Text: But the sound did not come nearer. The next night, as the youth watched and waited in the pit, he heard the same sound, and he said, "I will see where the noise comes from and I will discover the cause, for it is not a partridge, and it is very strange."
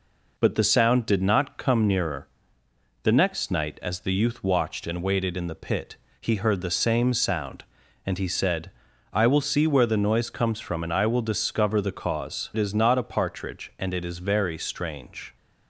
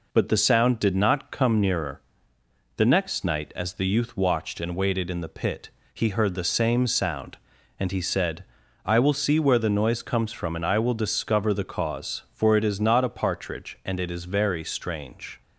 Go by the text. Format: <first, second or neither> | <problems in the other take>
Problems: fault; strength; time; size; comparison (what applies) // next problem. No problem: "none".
second | skips "for"; at 12.5 s